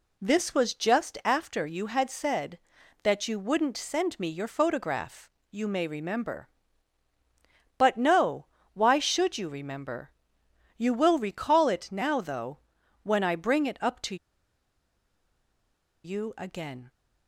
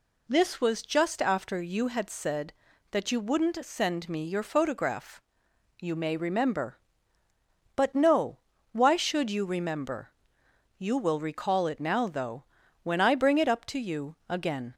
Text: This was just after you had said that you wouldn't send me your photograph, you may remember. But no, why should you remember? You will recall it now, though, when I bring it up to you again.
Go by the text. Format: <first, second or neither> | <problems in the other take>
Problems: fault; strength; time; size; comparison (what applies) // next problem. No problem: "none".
second | pauses between "to" and "you"; strong; at 14.1 s; 1.8 s long